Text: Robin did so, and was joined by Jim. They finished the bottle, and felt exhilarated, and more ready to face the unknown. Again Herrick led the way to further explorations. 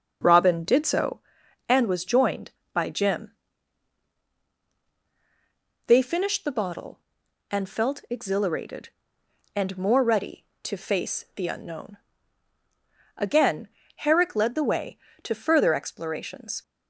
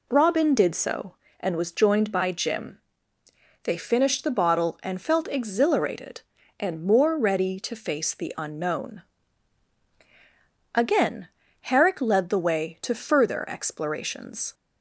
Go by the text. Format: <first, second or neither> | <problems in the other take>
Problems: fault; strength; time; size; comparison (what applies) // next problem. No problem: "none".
second | starts louder than the rest; noticeable; until 1.3 s; 5.5 dB // pauses between "Again" and "Herrick"; slight; at 13.6 s; 0.28 s long; slight in the second